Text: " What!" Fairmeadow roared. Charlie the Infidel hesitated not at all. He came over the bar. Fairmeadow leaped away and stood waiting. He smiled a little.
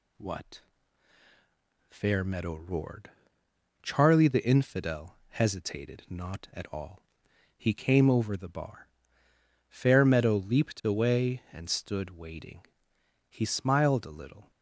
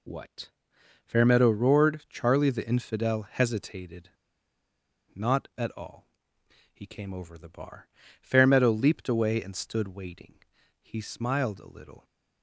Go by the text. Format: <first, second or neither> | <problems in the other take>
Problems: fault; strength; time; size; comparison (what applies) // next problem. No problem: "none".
first | pauses between "hesitated" and "not"; at 4.0 s; 1.0 s long